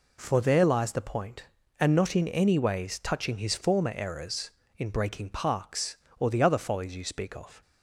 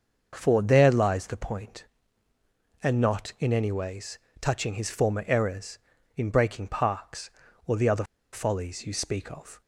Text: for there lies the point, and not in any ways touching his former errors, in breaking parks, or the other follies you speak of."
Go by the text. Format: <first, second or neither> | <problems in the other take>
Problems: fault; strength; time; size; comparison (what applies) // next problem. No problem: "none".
first | starts louder than the rest; until 1.3 s; 6.5 dB // pauses between "ways" and "touching"; slight; at 4.1 s; 0.22 s long // pauses between "other" and "follies"; slight; at 8.0 s; 0.28 s long